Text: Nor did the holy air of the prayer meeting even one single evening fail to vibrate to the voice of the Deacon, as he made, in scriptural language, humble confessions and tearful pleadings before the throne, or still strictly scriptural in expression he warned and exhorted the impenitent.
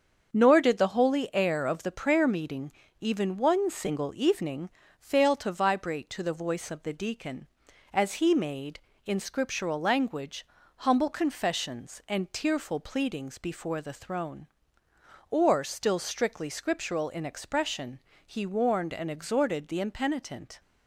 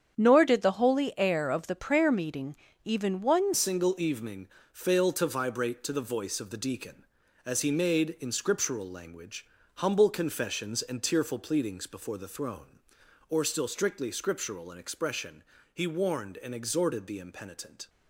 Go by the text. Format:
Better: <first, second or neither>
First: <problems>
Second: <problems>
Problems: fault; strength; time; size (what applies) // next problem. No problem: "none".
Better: first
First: starts louder than the rest; until 1.3 s; 7 dB // pauses between "meeting" and "even"; slight; at 2.7 s; 0.30 s long // pauses between "evening" and "fail"; slight; at 4.6 s; 0.32 s long // pauses between "expression" and "he"; slight; at 17.9 s; 0.26 s long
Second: starts louder than the rest; strong; until 1.1 s; 8 dB // pauses between "meeting" and "even"; slight; at 2.5 s; 0.30 s long // changes voice at "single"; from 3.5 s on; 14.3 s long // pauses between "evening" and "fail"; slight; at 4.4 s; 0.26 s long // pauses between "expression" and "he"; slight; at 15.4 s; 0.30 s long